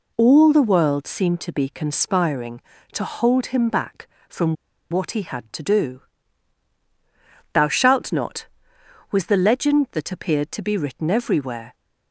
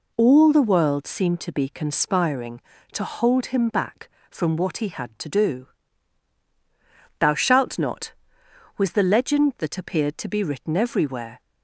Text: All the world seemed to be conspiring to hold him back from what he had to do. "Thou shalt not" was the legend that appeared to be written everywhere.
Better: second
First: pauses between "from" and "what"; at 4.5 s; 0.37 s long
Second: none

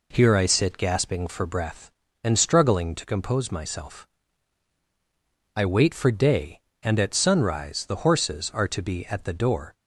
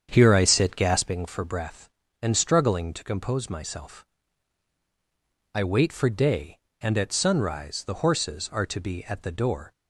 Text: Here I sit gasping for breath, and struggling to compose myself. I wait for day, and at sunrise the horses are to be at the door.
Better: first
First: none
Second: starts louder than the rest; strong; until 1.2 s; 7.5 dB

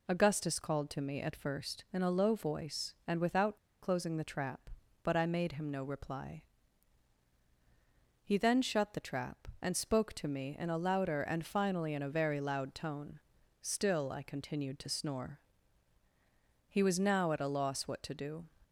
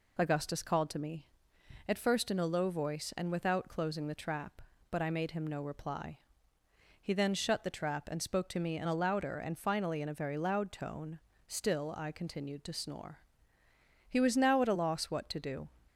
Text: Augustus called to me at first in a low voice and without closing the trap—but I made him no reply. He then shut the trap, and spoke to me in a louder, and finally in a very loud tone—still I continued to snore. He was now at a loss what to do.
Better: second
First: pauses between "without" and "closing"; slight; at 3.5 s; 0.26 s long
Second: none

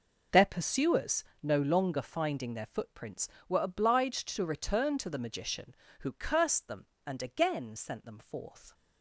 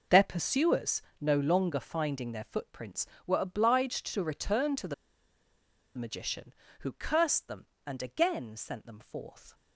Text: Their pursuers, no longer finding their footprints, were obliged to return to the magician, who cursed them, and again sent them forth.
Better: first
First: none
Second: pauses between "the" and "magician"; at 4.9 s; 1.0 s long

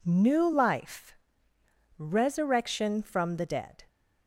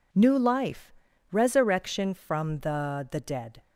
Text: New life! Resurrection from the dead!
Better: first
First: none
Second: says "the" twice; at 3.1 s

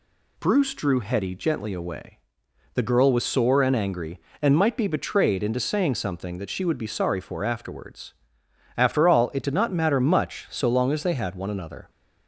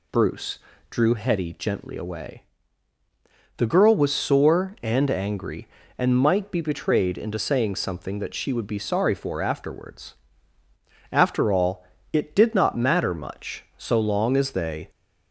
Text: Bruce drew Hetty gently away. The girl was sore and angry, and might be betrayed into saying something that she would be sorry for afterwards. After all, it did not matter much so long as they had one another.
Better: first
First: none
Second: pauses between "Bruce" and "drew"; slight; at 0.5 s; 0.30 s long // stops before "had one another"; at 14.8 s

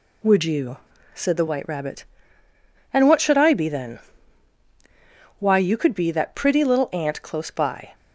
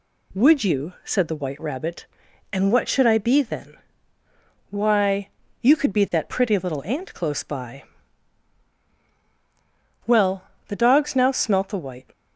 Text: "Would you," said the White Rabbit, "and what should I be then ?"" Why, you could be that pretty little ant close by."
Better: first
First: none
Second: goes on to say "Well the dogs now smelt the White"; strong; from 10.0 s on; 2.0 s long

